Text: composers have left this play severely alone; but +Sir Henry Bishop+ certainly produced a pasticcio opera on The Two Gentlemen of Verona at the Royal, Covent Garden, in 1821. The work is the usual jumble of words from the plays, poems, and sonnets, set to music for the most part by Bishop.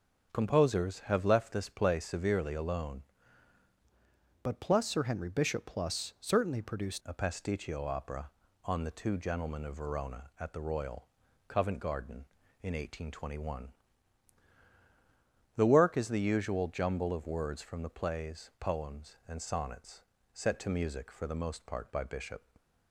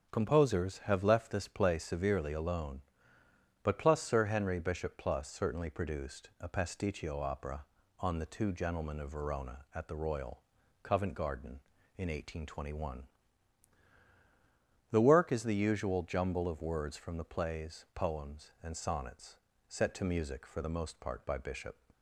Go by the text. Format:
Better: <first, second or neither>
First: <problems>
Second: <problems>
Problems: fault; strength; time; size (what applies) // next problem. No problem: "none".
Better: second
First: starts louder than the rest; strong; until 1.3 s; 7 dB // changes voice from "but" to "produced"; from 4.4 to 7.0 s; 2.6 s long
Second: starts louder than the rest; strong; until 1.1 s; 7.5 dB